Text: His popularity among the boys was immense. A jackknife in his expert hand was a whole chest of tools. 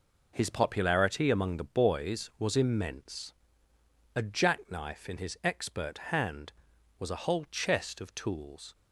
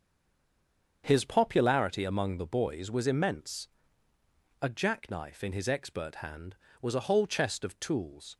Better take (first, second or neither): first